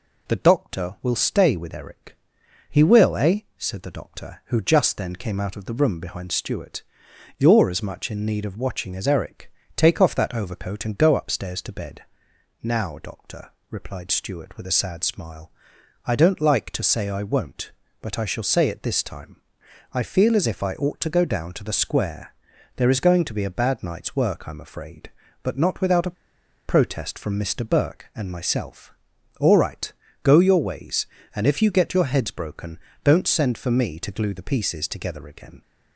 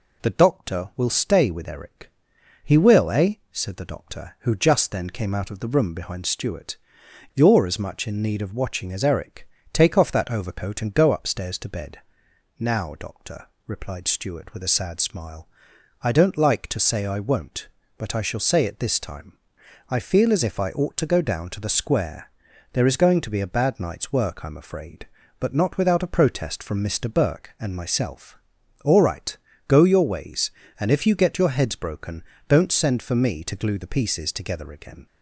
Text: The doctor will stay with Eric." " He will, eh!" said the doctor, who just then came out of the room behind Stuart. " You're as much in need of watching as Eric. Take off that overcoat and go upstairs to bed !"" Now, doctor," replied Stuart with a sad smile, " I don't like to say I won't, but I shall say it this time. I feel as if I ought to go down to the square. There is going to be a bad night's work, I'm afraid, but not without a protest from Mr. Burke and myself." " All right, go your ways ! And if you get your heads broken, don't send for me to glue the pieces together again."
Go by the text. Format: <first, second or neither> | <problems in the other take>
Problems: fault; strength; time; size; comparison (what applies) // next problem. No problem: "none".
second | pauses between "a" and "protest"; noticeable; at 26.1 s; 0.53 s long